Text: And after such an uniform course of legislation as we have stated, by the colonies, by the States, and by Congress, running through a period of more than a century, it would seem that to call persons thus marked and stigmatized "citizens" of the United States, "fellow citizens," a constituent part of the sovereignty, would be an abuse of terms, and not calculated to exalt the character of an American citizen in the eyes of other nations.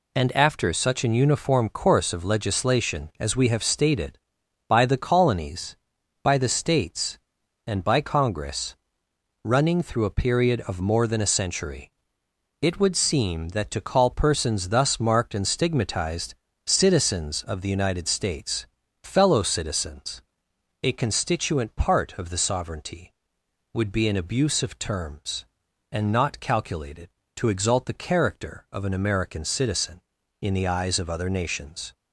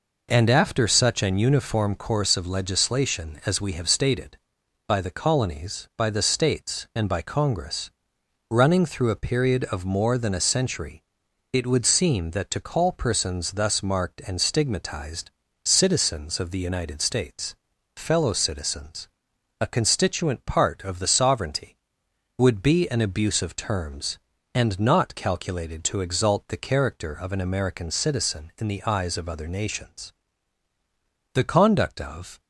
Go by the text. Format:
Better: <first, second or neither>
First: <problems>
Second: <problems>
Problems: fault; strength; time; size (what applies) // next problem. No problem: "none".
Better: first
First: pauses between "stigmatized" and "citizens"; slight; at 16.3 s; 0.32 s long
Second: pauses between "stigmatized" and "citizens"; slight; at 15.3 s; 0.32 s long // goes on to say "The conduct of"; noticeable; from 31.3 s on; 1.0 s long